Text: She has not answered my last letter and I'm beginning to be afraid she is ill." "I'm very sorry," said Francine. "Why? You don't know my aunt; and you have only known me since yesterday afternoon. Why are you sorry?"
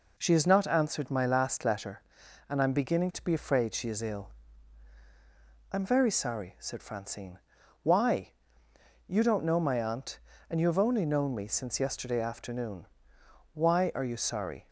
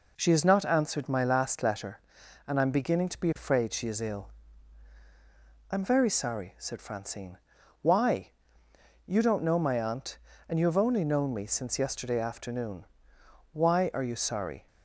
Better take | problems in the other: neither | none

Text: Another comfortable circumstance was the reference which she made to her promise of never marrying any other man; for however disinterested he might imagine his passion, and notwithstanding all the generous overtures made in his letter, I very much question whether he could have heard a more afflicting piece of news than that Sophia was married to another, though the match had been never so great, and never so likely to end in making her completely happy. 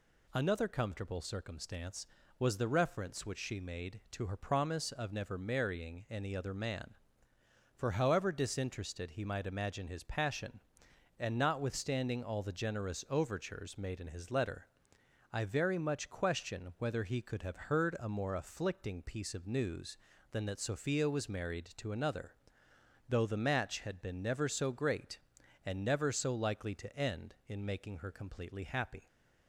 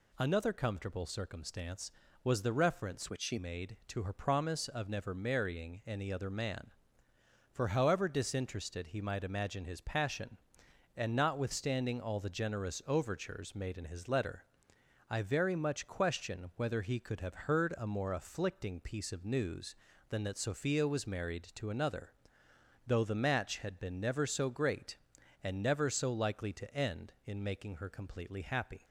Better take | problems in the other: first | changes voice from "which" to "she"; from 3.0 to 3.3 s; 0.3 s long

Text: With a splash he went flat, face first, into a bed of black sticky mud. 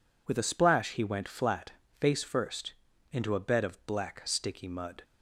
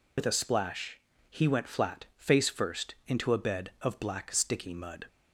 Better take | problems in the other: first | loses the start of "With"; at 0.1 s; 65 ms // pauses between "splash" and "he"; slight; at 0.9 s; 0.32 s long

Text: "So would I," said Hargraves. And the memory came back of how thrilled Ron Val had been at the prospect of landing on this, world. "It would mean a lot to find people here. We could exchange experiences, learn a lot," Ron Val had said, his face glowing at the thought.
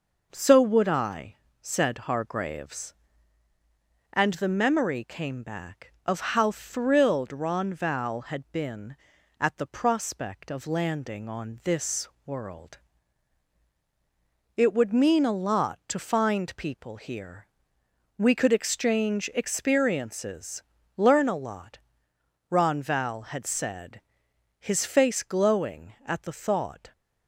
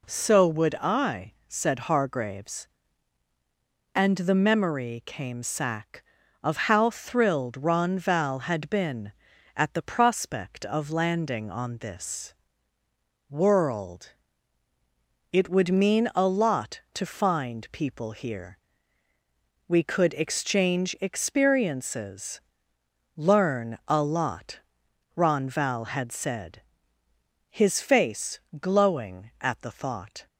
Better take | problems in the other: first | says "sack" for "back"; at 5.4 s // pauses between "face" and "glowing"; slight; at 28.4 s; 0.20 s long

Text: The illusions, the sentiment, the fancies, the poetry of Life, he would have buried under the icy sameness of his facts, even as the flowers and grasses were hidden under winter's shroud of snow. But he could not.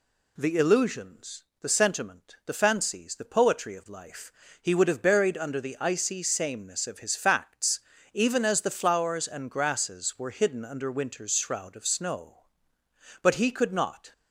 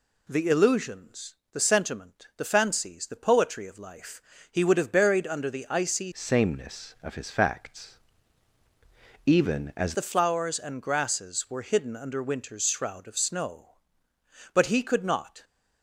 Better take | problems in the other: first | changes voice from "sameness" to "as"; from 6.1 to 9.9 s; 3.8 s long

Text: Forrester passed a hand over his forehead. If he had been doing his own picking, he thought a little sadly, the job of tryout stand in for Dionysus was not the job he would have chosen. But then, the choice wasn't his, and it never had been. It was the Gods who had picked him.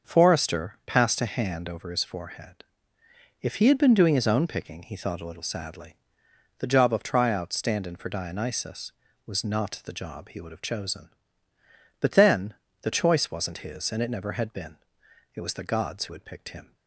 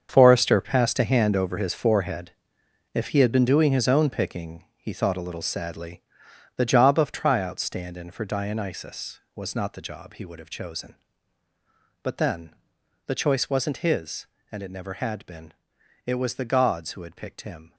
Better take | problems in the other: first | gets quieter; strong; throughout; 12 dB // starts louder than the rest; until 1.1 s; 7 dB; also in the first

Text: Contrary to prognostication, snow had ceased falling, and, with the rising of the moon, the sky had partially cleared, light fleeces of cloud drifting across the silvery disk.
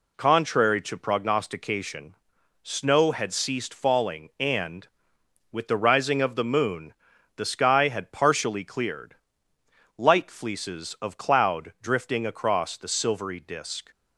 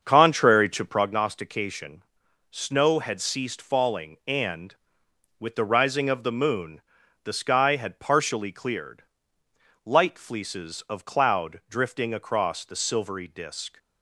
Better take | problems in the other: first | starts louder than the rest; until 1.2 s; 7 dB

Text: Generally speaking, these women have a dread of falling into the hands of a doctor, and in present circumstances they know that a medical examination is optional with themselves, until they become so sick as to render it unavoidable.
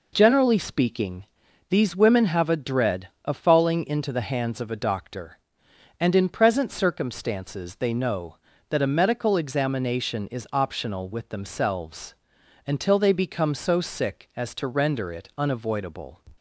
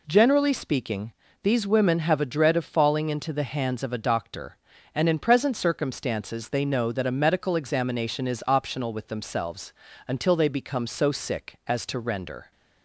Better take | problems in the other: first | stops before "it unavoidable"; at 12.5 s

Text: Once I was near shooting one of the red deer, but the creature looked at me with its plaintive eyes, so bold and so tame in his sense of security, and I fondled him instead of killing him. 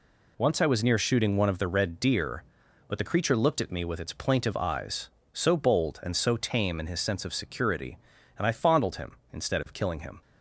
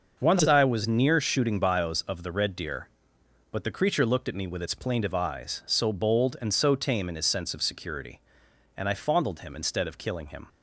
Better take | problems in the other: first | starts louder than the rest; noticeable; until 1.2 s; 6 dB // says "bios" for "one"; at 1.5 s

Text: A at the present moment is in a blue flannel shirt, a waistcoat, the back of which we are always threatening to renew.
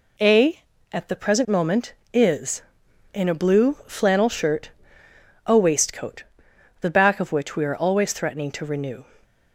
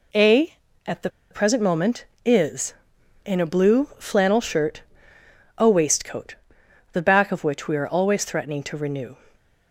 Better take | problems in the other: first | pauses between "the" and "present"; slight; at 1.0 s; 0.21 s long

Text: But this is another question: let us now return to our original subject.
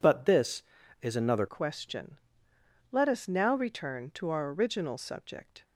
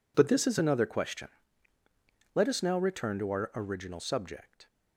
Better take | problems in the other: second | changes voice at "question"; from 1.4 s on; 4.2 s long

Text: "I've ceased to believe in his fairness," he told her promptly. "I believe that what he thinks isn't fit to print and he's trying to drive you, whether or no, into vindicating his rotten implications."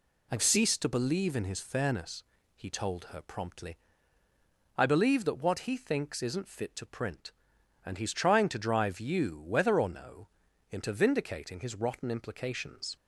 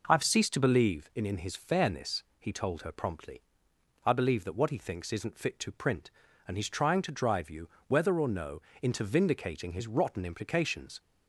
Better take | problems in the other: first | says "in" twice; at 1.2 s

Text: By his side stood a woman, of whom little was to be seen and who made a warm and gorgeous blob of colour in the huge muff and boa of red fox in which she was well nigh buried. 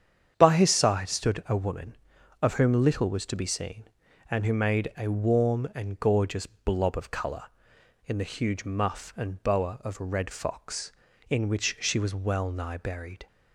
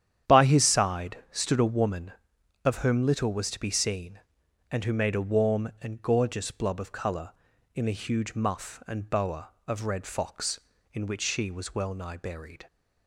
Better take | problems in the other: neither | starts louder than the rest; strong; the same in both

